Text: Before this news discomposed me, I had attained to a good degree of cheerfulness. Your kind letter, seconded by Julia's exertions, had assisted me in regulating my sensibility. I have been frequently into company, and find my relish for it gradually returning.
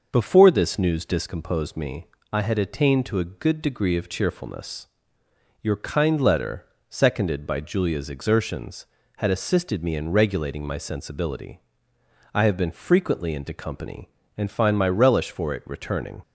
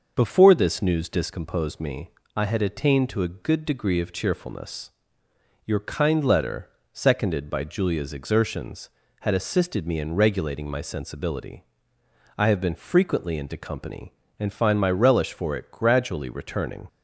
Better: second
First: skips "gradually"; at 15.6 s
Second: none

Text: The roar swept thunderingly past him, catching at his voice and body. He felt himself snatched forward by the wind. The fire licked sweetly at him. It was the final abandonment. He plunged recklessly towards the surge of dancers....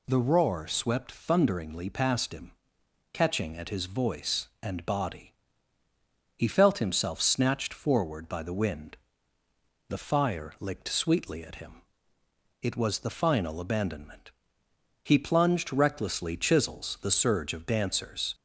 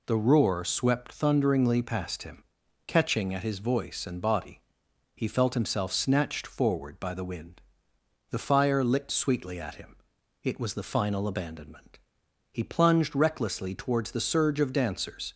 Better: second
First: says "chisels" for "towards"; at 16.3 s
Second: none

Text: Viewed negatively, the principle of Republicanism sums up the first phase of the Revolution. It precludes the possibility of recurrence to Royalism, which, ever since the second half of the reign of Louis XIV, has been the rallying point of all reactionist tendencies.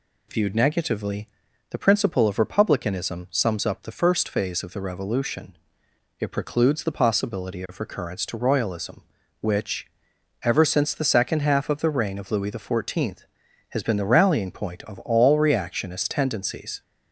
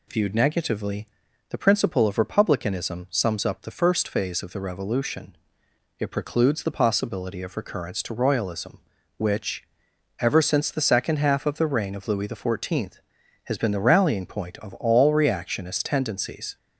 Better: neither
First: none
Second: none

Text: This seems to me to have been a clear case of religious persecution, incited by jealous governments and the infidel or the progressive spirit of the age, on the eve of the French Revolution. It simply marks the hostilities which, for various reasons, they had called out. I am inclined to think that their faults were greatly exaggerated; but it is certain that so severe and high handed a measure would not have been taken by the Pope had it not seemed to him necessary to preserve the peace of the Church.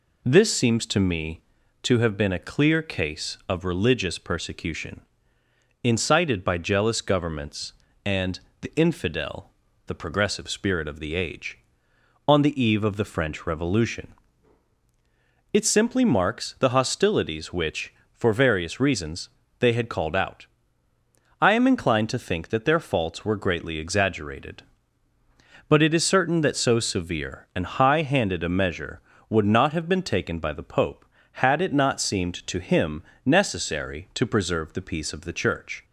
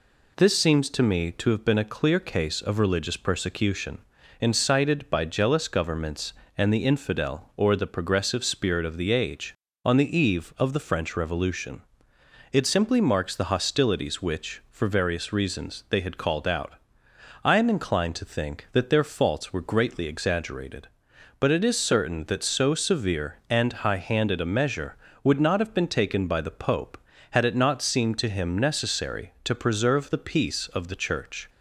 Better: second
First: pauses between "and" and "the"; slight; at 8.3 s; 0.22 s long // skips "or"; at 9.6 s // pauses between "him" and "necessary"; slight; at 33.0 s; 0.22 s long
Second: none

